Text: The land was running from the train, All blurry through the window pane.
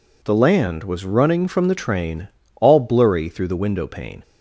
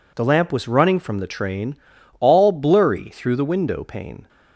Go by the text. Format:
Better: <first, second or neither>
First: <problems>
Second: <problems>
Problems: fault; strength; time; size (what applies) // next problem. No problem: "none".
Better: first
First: none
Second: says "lamp" for "land"; at 0.2 s